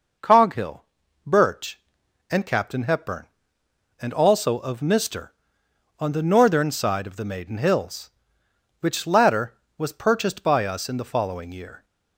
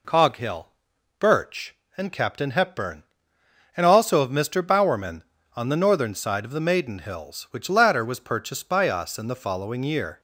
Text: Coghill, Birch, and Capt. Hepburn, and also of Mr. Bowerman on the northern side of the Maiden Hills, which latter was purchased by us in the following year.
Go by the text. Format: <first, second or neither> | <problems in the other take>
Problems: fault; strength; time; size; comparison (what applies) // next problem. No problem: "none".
second | skips "Bowerman"; at 5.6 s